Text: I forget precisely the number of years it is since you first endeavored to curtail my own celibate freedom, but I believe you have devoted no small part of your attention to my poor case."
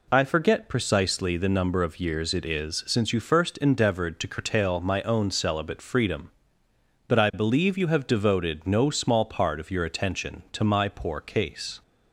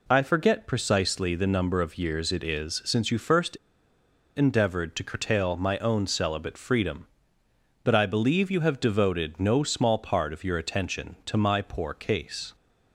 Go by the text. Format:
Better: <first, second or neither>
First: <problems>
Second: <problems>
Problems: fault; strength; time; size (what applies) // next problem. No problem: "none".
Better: first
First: none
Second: pauses between "first" and "endeavored"; noticeable; at 3.5 s; 0.78 s long